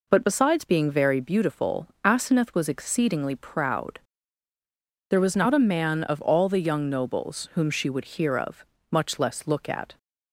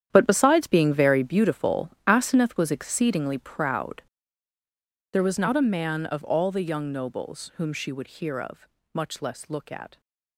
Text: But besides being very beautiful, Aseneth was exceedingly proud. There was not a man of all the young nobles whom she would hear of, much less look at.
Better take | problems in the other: first | gets quieter; strong; throughout; 14.5 dB

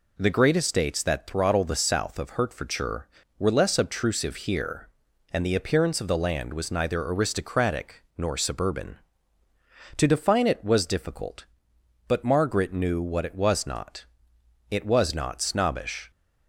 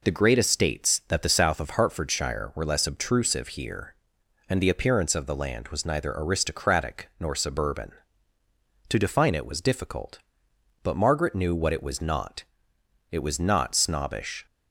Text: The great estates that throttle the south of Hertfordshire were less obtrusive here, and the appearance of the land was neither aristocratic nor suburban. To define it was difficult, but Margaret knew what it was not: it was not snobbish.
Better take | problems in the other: first | skips "throttle"; at 1.2 s

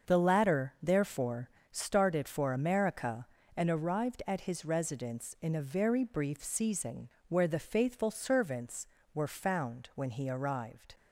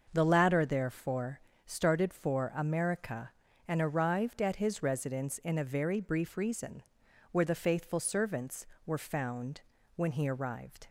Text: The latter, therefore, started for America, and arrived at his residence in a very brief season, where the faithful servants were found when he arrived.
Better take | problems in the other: first | starts louder than the rest; until 1.1 s; 6.5 dB; also in the first // says "reason" for "season"; at 6.3 s // pauses between "found" and "when"; slight; at 9.6 s; 0.36 s long

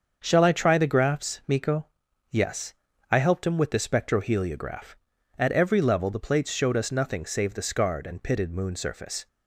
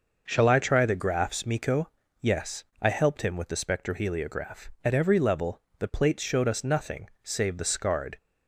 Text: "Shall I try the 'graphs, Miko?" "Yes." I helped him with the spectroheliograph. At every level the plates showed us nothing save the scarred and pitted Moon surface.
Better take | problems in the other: first | starts louder than the rest; noticeable; until 1.2 s; 6 dB; also in the first // pauses between "level" and "the"; slight; at 5.6 s; 0.16 s long // stops before "and pitted Moon surface"; at 8.1 s

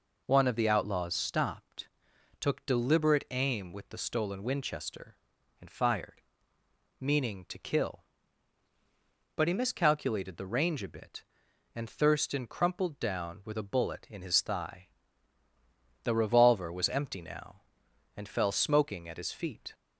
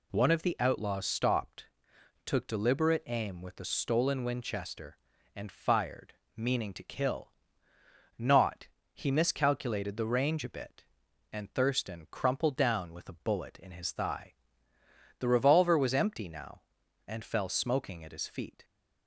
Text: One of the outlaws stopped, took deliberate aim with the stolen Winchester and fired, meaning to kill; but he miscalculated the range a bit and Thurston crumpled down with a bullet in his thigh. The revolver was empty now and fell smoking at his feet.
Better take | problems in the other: first | says "not" for "but"; at 8.1 s

